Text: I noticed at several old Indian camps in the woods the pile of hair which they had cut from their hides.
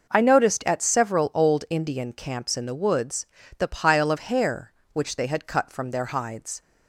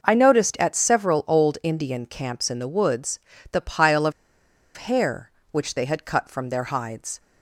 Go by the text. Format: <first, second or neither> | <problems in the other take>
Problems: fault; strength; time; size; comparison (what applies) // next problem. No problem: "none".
first | pauses between "woods" and "the"; slight; at 3.1 s; 0.32 s long; slight in the first // pauses between "of" and "hair"; noticeable; at 4.1 s; 0.64 s long